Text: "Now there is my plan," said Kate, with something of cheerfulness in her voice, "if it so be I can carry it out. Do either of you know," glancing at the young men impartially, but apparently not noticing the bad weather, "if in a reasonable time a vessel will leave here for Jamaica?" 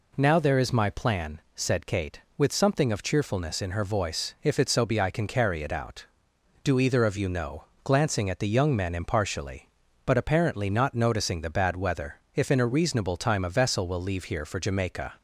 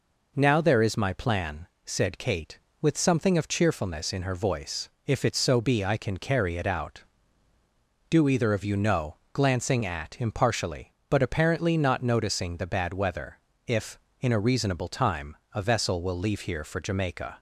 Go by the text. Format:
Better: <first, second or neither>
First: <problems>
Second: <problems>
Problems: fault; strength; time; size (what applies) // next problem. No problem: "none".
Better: first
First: none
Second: skips "the young men"; at 10.1 s // pauses between "time" and "a"; slight; at 15.3 s; 0.16 s long